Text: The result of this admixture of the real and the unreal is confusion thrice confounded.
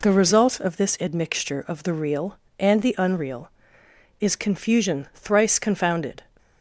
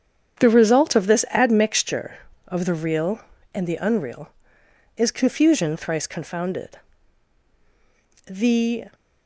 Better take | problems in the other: first | starts louder than the rest; strong; until 1.4 s; 8.5 dB // goes on to say "The"; noticeable; from 8.2 s on; 0.62 s long

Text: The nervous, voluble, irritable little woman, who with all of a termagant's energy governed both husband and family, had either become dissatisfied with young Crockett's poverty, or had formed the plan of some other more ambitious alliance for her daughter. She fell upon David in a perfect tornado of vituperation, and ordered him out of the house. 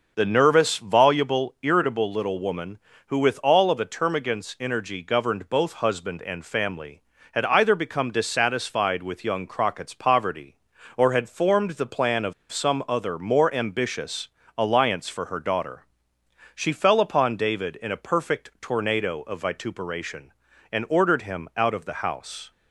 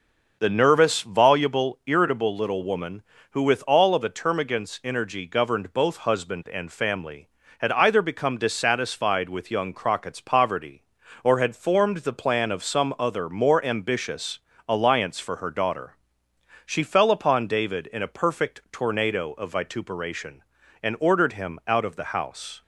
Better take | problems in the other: second | starts louder than the rest; noticeable; until 1.1 s; 6 dB; noticeable in the second // pauses between "of" and "some"; slight; at 12.3 s; 0.18 s long // pauses between "ambitious" and "alliance"; slight; at 14.2 s; 0.32 s long; slight in the second

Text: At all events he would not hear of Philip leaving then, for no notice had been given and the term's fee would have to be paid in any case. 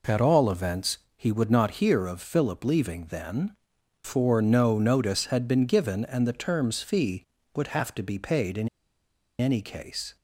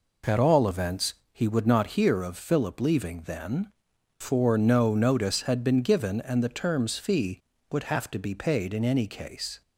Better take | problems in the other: second | pauses between "events" and "he"; slight; at 0.9 s; 0.18 s long; slight in the second // pauses between "in" and "any"; noticeable; at 8.6 s; 0.71 s long

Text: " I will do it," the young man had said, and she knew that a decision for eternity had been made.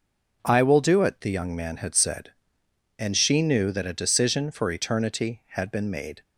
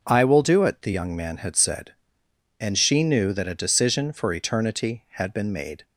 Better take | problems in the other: neither | none

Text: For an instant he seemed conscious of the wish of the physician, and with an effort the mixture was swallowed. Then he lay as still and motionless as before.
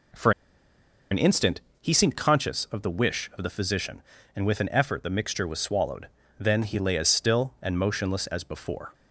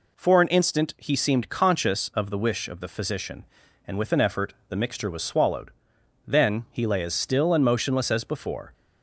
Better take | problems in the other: second | pauses between "For" and "an"; noticeable; at 0.3 s; 0.80 s long // pauses between "instant" and "he"; slight; at 1.6 s; 0.20 s long

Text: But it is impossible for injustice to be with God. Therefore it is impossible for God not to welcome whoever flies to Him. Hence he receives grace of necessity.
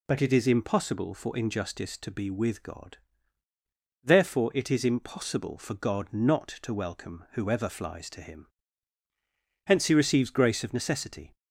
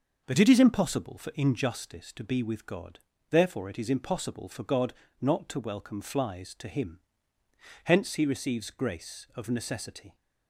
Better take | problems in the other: first | starts louder than the rest; noticeable; until 1.2 s; 6 dB // pauses between "God" and "not"; slight; at 4.9 s; 0.26 s long // skips "whoever"; at 5.9 s

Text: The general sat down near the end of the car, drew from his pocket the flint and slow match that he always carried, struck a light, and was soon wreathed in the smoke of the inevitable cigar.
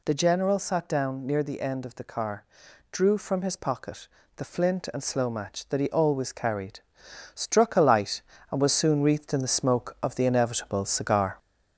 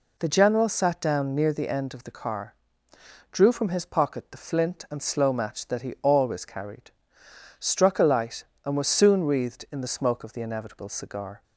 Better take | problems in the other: second | gets louder; slight; throughout; 3.5 dB // pauses between "pocket" and "the"; slight; at 4.0 s; 0.26 s long

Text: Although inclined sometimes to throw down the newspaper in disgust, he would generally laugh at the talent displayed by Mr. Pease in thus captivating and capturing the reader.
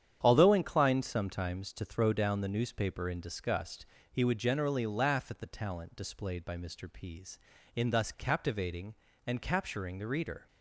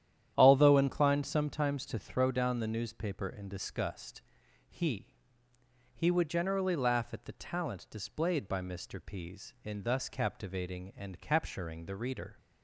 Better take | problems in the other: first | starts louder than the rest; strong; until 1.3 s; 10.5 dB; strong in the first // says "he" twice; at 5.9 s

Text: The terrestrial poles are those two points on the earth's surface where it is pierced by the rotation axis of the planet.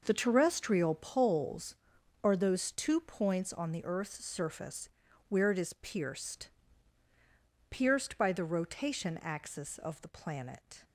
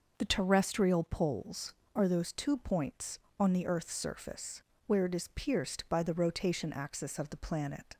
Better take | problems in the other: second | pauses between "surface" and "where"; at 4.8 s; 0.40 s long; slight in the second // says "pierced" twice; at 7.6 s

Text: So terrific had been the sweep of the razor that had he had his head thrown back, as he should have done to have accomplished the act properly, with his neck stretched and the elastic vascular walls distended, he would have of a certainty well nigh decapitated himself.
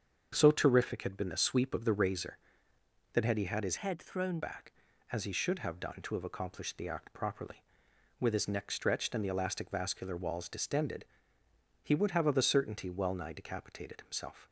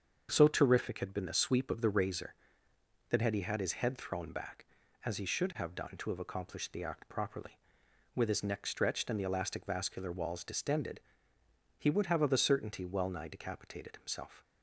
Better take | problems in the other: second | starts louder than the rest; until 1.3 s; 7 dB; also in the second // changes voice from "head" to "thrown"; from 3.7 to 4.4 s; 0.7 s long

